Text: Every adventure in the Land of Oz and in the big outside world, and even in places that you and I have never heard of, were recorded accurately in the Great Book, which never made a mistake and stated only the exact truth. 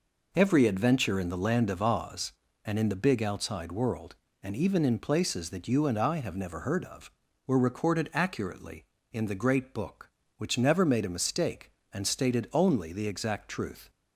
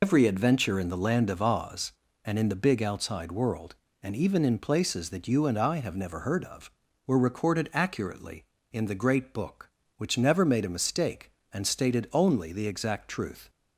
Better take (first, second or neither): first